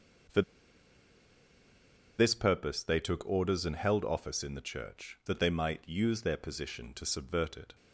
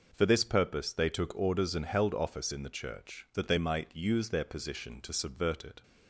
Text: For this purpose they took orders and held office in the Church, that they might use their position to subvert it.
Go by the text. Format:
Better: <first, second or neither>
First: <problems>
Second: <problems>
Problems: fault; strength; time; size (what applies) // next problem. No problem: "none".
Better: second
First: pauses between "For" and "this"; strong; at 0.4 s; 1.7 s long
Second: none